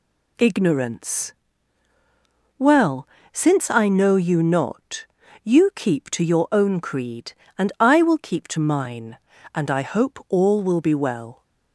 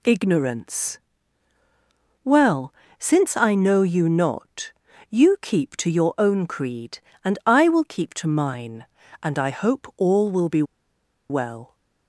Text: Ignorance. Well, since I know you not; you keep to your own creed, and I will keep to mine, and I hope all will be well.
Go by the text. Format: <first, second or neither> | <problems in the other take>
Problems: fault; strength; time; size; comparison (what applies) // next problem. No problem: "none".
first | pauses between "be" and "well"; noticeable; at 10.6 s; 0.66 s long